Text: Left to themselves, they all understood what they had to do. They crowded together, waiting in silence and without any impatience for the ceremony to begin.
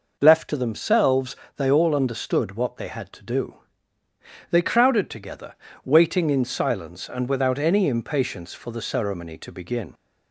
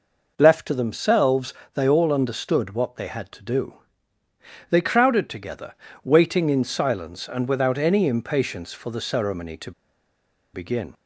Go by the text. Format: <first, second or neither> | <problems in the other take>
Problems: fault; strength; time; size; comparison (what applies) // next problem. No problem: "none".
first | pauses between "to" and "begin"; noticeable; at 9.7 s; 0.82 s long